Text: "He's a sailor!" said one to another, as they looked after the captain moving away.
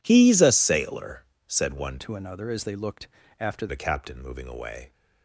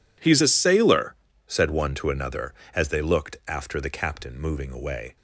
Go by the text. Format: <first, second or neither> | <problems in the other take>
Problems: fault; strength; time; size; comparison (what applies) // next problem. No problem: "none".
second | changes voice from "to" to "after"; from 1.9 to 3.6 s; 1.7 s long // pauses between "looked" and "after"; slight; at 3.0 s; 0.32 s long